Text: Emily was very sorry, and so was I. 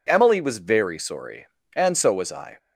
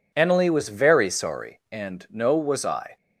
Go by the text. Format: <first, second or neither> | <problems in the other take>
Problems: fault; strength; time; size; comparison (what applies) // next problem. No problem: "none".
first | says "no" for "so"; at 2.1 s